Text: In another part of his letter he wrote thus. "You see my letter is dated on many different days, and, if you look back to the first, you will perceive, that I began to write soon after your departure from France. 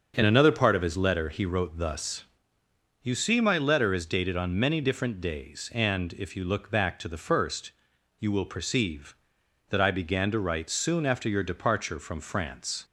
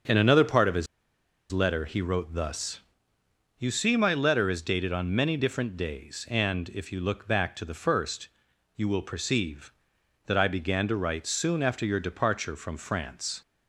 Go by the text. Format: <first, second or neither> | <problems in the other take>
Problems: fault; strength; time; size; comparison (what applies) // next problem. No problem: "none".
first | starts louder than the rest; until 1.7 s; 6.5 dB; also in the first // pauses between "his" and "letter"; noticeable; at 0.8 s; 0.65 s long